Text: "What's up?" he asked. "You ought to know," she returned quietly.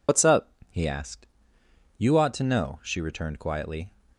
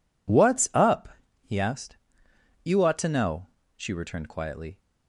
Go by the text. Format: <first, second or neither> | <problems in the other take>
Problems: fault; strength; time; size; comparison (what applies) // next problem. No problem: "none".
second | loses the start of "What's"; at 0.0 s; 70 ms